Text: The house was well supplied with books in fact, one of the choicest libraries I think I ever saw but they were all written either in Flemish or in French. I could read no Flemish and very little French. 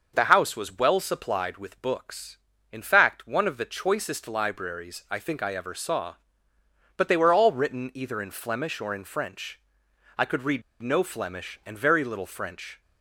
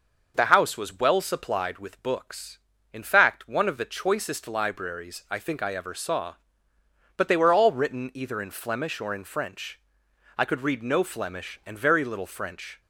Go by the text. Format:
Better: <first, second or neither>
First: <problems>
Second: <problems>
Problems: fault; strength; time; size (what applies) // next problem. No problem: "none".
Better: second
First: pauses between "read" and "no"; slight; at 10.6 s; 0.18 s long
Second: none